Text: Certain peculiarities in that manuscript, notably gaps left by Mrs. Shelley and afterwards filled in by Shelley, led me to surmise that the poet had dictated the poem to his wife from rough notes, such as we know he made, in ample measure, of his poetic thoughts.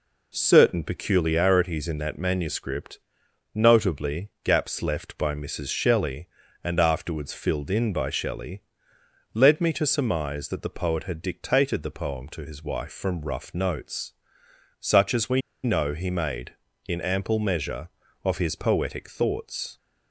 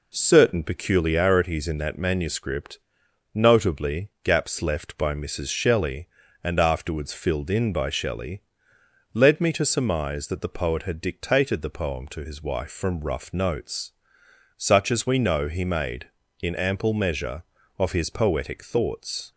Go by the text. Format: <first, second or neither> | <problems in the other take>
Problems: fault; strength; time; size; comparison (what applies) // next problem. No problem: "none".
second | pauses between "we" and "know"; slight; at 15.4 s; 0.23 s long